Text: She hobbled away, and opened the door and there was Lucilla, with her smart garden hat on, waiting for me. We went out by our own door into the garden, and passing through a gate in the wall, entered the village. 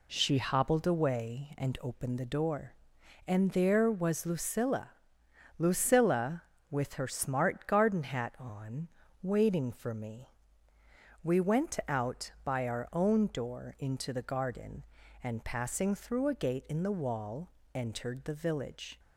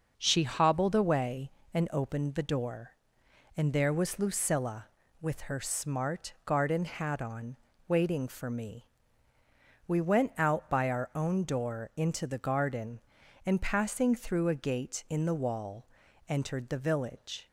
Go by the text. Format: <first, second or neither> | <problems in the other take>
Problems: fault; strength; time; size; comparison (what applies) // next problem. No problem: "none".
second | says "Lucilla" twice; at 5.5 s